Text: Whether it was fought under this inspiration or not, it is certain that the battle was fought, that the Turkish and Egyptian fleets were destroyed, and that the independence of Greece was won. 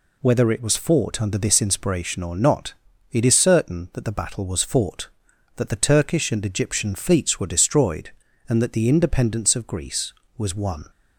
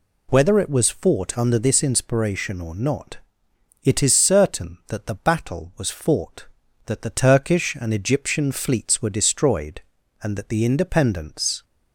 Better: first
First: none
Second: stops before "of Greece was won"; at 11.6 s

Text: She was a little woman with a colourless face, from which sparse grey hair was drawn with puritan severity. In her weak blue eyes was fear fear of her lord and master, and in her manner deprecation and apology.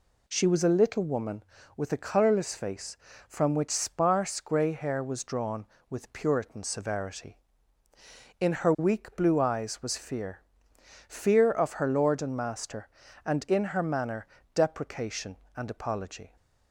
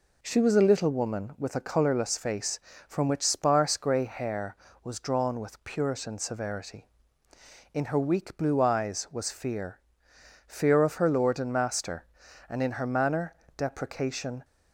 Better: first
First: pauses between "fear" and "fear"; noticeable; at 10.3 s; 0.68 s long // pauses between "manner" and "deprecation"; slight; at 14.2 s; 0.26 s long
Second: pauses between "fear" and "fear"; noticeable; at 9.7 s; 0.68 s long // pauses between "manner" and "deprecation"; slight; at 13.3 s; 0.24 s long // stops before "and apology"; at 14.4 s

